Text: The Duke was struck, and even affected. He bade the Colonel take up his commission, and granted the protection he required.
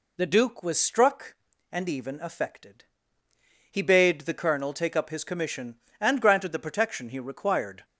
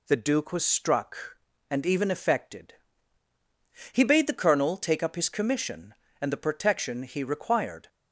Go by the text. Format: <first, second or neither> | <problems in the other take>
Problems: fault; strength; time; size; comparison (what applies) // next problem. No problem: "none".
first | skips "granted"; at 6.3 s